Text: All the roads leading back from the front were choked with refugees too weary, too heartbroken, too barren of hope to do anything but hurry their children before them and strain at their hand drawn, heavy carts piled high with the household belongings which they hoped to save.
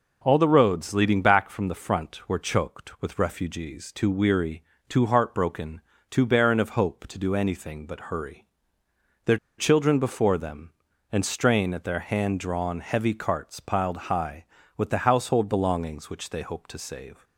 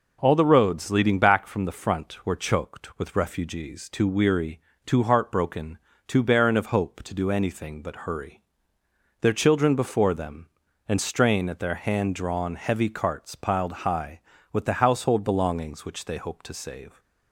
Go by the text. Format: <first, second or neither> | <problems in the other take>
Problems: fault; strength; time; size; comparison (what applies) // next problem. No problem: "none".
second | pauses between "hurry" and "their"; noticeable; at 8.4 s; 0.78 s long; noticeable in the second // pauses between "their" and "children"; slight; at 9.3 s; 0.21 s long